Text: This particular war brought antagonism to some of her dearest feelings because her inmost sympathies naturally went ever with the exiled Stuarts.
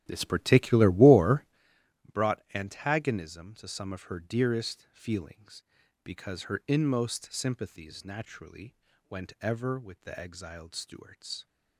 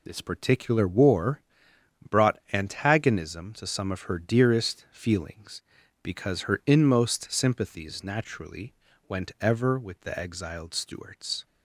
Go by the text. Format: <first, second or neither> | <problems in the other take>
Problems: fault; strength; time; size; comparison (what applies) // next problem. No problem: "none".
second | starts louder than the rest; strong; until 1.7 s; 12 dB // pauses between "war" and "brought"; noticeable; at 1.4 s; 0.68 s long; noticeable in the second // pauses between "naturally" and "went"; slight; at 8.7 s; 0.34 s long; slight in the second